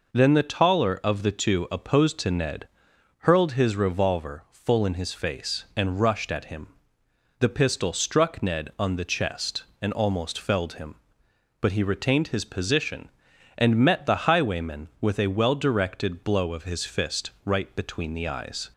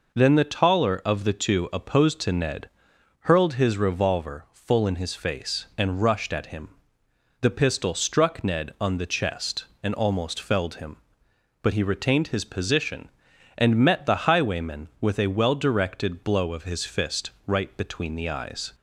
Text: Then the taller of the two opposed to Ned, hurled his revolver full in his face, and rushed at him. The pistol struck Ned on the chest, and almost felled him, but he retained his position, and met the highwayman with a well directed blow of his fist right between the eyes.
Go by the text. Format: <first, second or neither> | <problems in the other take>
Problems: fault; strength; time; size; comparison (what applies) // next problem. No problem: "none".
neither | none